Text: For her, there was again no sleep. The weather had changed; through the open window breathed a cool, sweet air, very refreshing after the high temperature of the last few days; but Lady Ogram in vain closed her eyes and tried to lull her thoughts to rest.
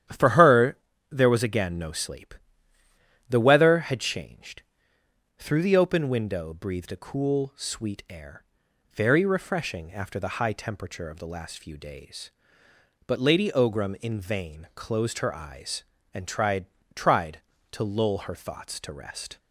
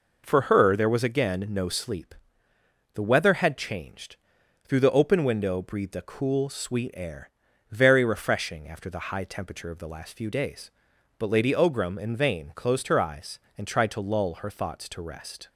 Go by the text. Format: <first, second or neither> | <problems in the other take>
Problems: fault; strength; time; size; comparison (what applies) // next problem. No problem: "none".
second | starts louder than the rest; strong; until 1.4 s; 10.5 dB // says "tried" twice; at 16.9 s